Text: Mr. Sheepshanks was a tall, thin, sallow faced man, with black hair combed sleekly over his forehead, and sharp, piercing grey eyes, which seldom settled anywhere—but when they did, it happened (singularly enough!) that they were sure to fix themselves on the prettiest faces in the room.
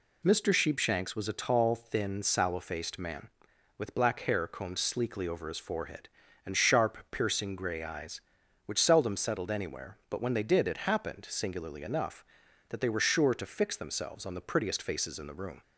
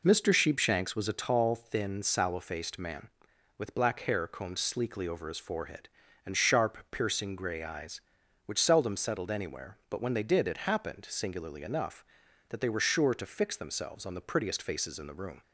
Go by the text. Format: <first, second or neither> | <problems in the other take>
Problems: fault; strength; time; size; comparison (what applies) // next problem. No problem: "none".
first | starts louder than the rest; noticeable; until 1.4 s; 4 dB